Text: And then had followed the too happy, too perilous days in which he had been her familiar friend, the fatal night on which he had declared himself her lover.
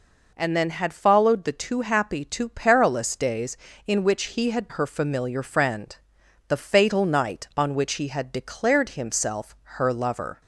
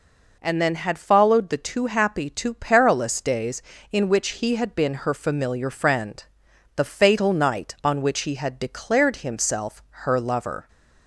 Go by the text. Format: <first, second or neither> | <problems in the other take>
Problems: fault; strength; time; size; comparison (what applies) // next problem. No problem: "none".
second | skips "been"; at 4.6 s